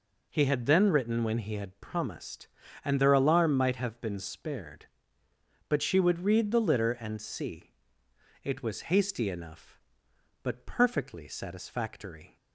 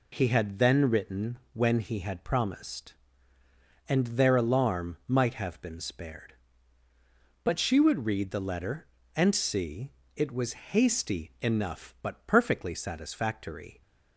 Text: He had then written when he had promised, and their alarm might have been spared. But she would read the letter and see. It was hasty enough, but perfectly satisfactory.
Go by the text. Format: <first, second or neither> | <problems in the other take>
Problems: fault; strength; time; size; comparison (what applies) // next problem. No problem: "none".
second | says "litter" for "letter"; at 6.5 s